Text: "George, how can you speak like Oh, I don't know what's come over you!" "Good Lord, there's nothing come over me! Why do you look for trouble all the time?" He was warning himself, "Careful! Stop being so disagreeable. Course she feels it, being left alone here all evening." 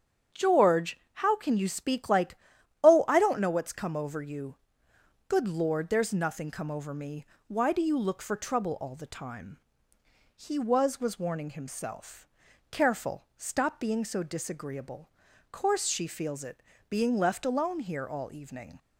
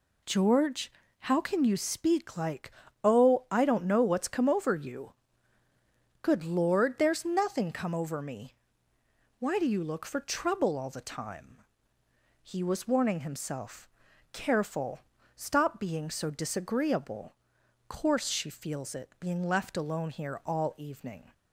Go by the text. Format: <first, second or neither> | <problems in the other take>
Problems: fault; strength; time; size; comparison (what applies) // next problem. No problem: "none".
second | starts louder than the rest; strong; until 1.4 s; 8.5 dB // pauses between "like" and "Oh"; noticeable; at 2.3 s; 0.46 s long; slight in the second // says "was" twice; at 11.0 s